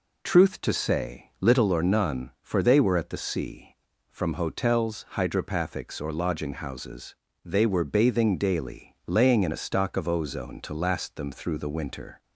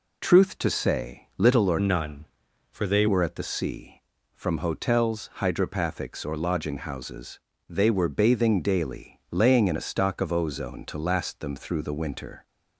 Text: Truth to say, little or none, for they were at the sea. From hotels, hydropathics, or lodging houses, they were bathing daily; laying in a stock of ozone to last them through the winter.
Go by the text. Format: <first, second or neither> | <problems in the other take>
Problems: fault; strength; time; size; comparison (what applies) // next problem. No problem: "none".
first | changes voice from "none" to "they"; from 1.7 to 3.0 s; 1.3 s long